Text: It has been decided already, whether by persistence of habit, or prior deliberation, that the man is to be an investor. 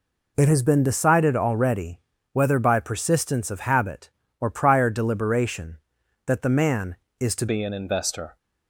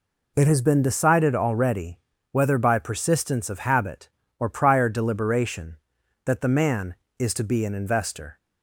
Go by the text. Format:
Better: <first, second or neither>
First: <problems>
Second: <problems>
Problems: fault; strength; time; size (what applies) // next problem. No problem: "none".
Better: second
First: changes voice at "be"; from 7.4 s on; 0.9 s long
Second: none